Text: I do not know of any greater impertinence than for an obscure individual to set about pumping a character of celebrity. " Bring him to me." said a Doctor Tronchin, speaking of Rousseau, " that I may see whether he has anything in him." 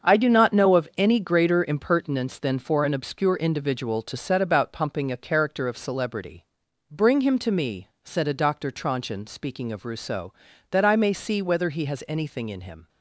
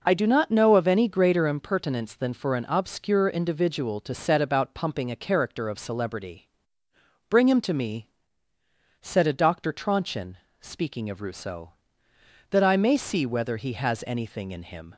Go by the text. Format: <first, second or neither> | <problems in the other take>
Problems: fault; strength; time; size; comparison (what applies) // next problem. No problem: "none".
second | gets quieter; strong; throughout; 10.5 dB // starts louder than the rest; strong; until 1.1 s; 7 dB; also in the second